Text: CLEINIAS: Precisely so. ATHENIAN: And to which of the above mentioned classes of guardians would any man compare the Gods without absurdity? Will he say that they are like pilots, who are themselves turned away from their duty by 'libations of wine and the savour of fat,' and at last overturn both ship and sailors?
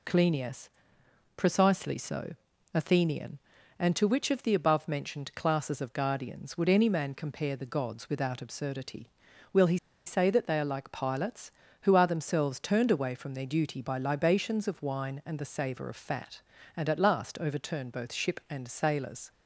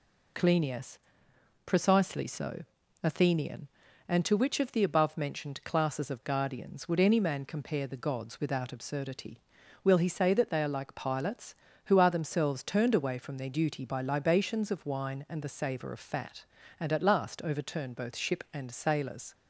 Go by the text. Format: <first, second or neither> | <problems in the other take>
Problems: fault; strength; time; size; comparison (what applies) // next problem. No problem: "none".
second | pauses between "he" and "say"; slight; at 9.7 s; 0.29 s long